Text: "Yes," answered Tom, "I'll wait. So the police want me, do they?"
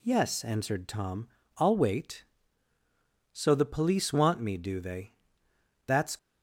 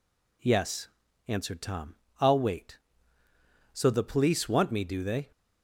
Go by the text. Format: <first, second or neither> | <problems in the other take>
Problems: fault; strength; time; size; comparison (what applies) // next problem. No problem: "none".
second | goes on to say "That's"; slight; from 5.8 s on; 0.32 s long